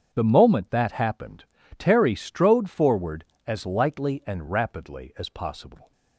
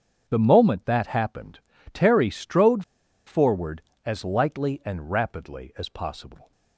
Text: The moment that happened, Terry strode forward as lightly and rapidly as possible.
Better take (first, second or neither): first